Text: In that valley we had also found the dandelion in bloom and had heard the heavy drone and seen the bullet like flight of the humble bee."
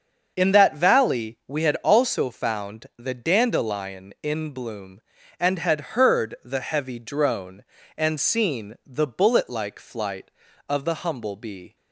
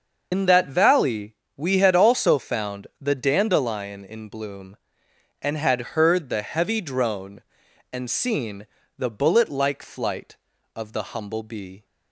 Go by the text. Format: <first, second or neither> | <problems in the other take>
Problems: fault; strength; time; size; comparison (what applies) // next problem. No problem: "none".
first | loses the start of "In"; at 0.3 s; 95 ms // starts louder than the rest; until 1.3 s; 6.5 dB; also in the first // pauses between "valley" and "we"; slight; at 1.3 s; 0.22 s long // pauses between "seen" and "the"; slight; at 8.6 s; 0.32 s long